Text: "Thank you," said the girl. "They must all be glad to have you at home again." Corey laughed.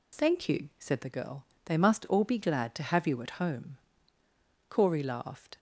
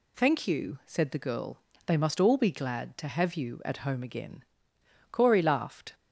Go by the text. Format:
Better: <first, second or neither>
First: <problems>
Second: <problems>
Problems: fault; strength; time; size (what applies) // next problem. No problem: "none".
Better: second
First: skips "again"; at 4.2 s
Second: none